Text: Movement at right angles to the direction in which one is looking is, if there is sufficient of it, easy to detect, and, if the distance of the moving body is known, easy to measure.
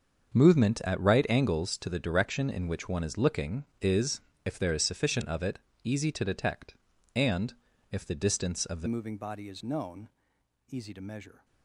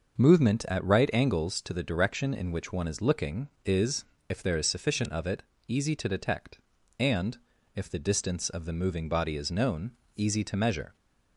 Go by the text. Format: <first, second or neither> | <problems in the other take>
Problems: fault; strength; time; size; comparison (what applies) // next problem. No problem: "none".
second | starts louder than the rest; until 1.3 s; 6.5 dB // changes voice at "moving"; from 8.8 s on; 2.6 s long